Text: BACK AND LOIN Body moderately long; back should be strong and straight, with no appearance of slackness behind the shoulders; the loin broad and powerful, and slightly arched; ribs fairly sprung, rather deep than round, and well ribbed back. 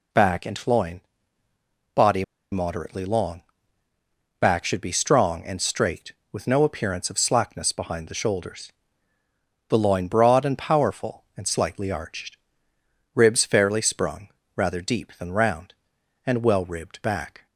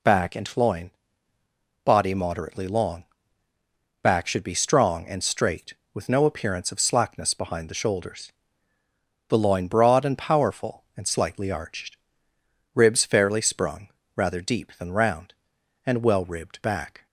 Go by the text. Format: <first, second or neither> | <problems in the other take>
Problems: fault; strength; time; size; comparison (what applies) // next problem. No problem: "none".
second | pauses between "LOIN" and "Body"; noticeable; at 1.0 s; 0.92 s long; noticeable in the second // pauses between "Body" and "moderately"; slight; at 2.2 s; 0.27 s long